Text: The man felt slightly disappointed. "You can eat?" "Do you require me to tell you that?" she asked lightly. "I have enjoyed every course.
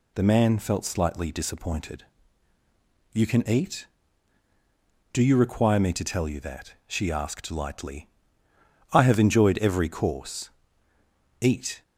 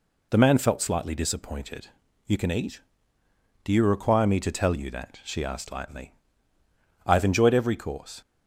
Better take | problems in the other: second | goes on to say "Eat"; slight; from 11.4 s on; 0.42 s long

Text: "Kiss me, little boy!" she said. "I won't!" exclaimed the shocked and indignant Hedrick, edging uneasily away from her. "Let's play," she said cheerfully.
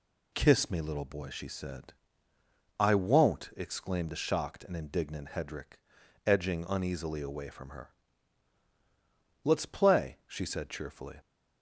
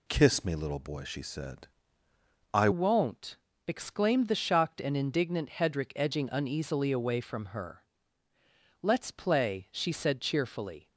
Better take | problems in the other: first | changes voice at "won't"; from 2.7 s on; 8.1 s long

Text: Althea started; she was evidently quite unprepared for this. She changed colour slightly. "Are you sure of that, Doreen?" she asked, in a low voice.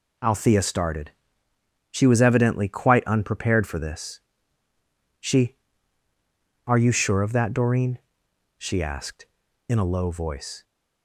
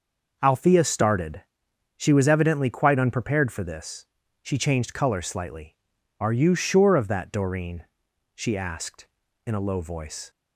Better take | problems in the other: second | skips "changed colour slightly"; at 6.0 s

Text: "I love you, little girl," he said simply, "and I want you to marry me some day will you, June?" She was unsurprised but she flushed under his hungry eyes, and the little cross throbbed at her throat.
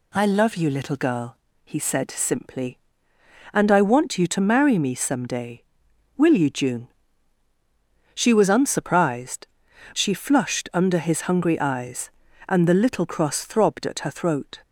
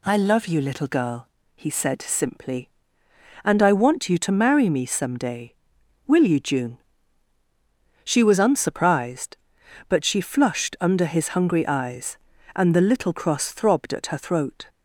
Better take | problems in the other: second | skips "but"; at 9.7 s

